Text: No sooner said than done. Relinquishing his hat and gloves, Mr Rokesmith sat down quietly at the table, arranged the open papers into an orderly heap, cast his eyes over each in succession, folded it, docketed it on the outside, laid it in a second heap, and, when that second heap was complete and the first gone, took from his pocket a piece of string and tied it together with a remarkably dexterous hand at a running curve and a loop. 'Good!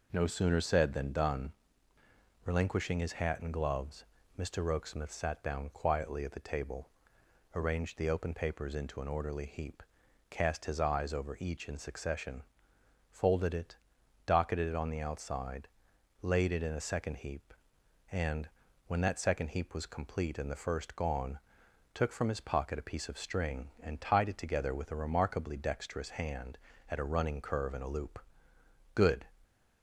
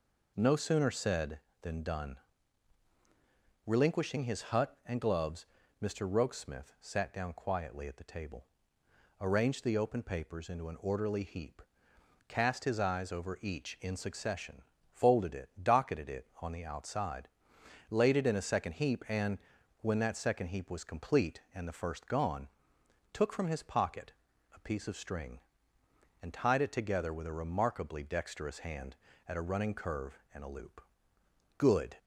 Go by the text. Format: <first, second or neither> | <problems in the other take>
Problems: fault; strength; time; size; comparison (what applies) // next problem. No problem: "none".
first | says "hut" for "hat"; at 4.4 s // pauses between "pocket" and "a"; at 24.1 s; 0.42 s long